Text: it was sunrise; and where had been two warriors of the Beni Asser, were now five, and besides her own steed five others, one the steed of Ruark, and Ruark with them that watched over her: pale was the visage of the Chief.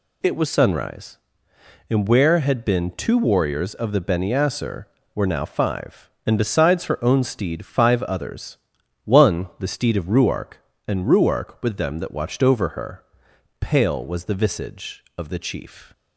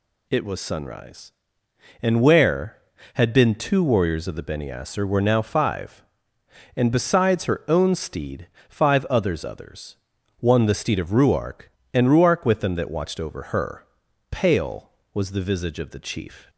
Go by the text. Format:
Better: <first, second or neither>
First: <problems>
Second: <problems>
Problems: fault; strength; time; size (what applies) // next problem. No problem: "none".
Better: first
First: none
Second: pauses between "steed" and "five"; slight; at 8.4 s; 0.20 s long // says "others" twice; at 9.4 s